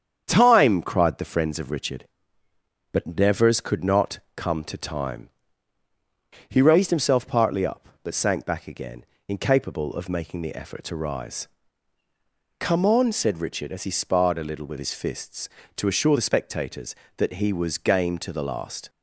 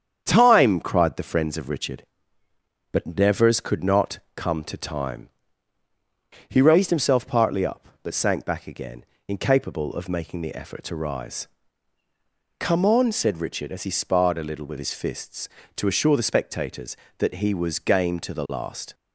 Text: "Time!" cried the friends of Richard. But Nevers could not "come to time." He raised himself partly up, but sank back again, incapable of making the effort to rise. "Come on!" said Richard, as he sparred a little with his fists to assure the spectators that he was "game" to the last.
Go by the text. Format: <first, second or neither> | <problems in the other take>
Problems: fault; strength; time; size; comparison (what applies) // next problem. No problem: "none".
neither | starts louder than the rest; strong; the same in both // pauses between "not" and "come"; slight; the same in both